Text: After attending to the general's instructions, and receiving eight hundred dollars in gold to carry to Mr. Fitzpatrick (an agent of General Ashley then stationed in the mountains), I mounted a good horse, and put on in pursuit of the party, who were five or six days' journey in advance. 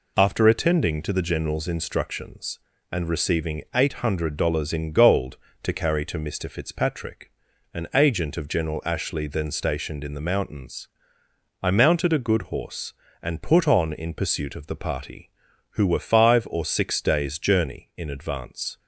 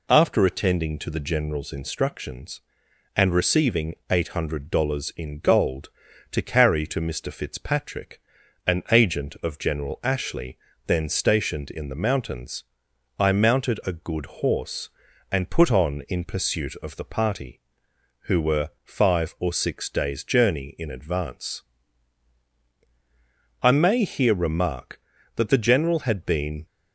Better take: first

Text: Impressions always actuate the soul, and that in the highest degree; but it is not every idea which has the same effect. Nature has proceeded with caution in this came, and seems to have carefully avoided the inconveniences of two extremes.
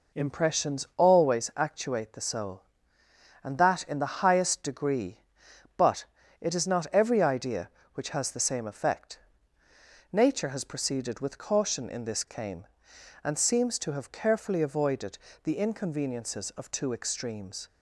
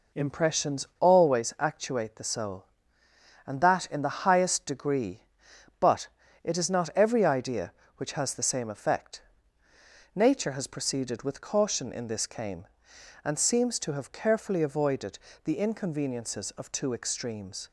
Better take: neither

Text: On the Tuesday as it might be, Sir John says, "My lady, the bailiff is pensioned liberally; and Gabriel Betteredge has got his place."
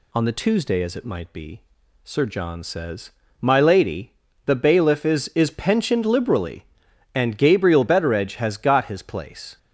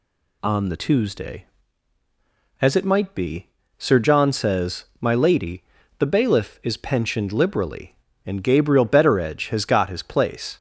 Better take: second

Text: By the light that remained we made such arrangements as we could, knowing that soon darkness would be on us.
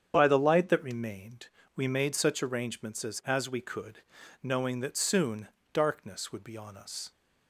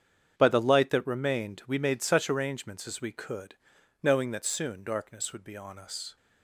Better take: second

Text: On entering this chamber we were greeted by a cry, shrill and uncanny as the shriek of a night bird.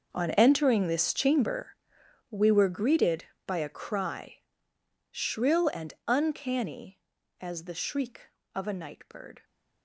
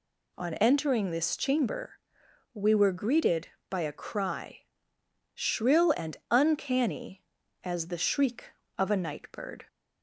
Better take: second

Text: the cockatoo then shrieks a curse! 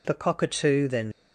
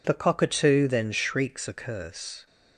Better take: second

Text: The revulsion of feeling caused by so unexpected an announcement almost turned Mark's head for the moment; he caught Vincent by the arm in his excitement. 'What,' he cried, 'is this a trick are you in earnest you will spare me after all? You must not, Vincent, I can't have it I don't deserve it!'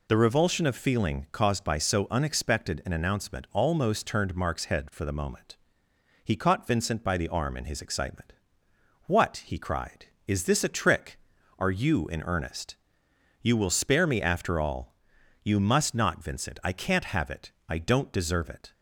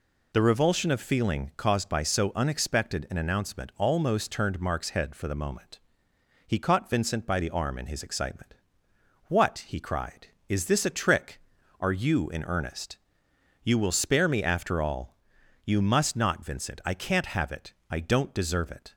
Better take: neither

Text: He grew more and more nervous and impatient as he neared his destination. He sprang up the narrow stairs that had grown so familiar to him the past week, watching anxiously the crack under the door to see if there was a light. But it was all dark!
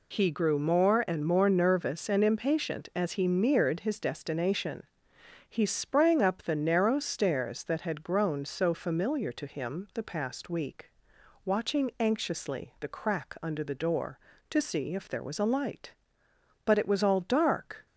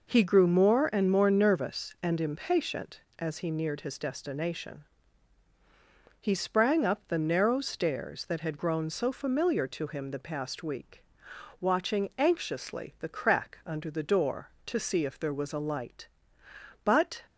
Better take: first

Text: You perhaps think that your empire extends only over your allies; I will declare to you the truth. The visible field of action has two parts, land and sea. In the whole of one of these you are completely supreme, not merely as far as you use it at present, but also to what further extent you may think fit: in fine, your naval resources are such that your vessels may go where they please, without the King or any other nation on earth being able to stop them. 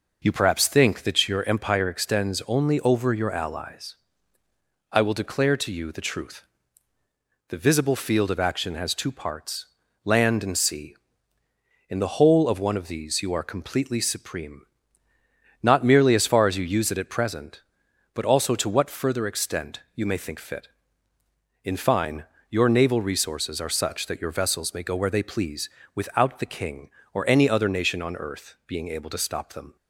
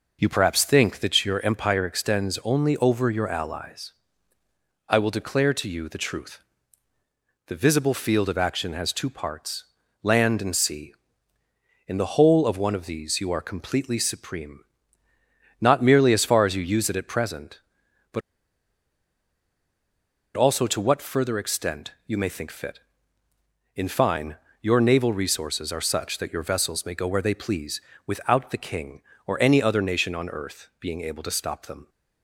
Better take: first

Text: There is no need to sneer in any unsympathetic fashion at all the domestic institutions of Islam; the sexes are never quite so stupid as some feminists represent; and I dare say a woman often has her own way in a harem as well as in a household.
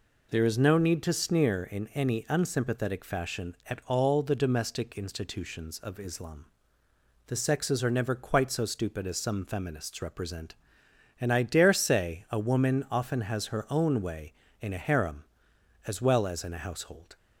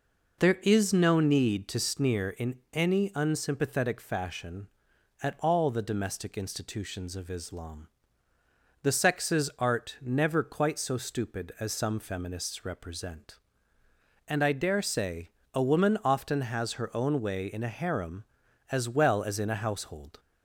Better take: first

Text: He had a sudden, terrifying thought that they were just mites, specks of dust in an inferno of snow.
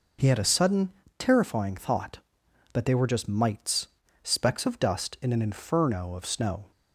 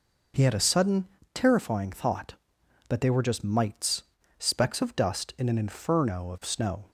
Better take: neither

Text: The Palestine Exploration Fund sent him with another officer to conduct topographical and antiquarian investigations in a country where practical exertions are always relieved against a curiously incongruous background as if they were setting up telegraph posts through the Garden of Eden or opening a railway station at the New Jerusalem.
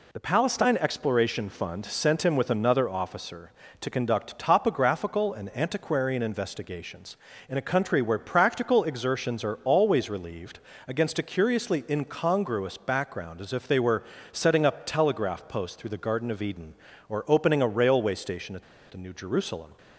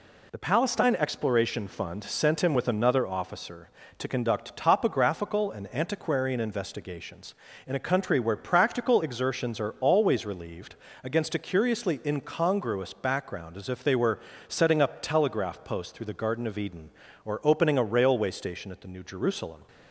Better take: second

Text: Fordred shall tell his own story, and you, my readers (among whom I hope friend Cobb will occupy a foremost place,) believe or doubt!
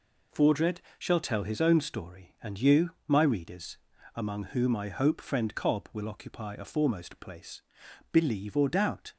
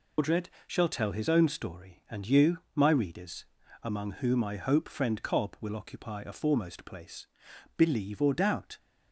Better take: first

